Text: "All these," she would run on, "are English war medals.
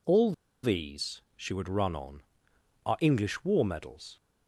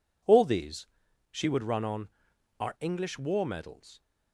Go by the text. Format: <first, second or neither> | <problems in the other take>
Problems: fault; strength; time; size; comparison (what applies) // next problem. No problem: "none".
second | pauses between "All" and "these"; slight; at 0.3 s; 0.31 s long